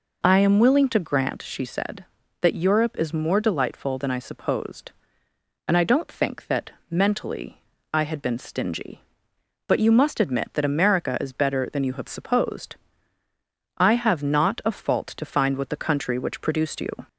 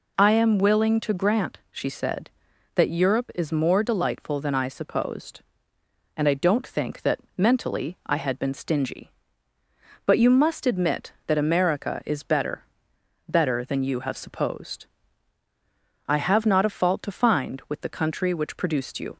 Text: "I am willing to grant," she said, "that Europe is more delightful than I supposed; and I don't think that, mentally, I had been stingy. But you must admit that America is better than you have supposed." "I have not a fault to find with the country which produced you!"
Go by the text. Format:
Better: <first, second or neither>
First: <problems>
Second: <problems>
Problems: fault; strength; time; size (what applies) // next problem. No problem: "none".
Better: first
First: none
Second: says "better" twice; at 13.2 s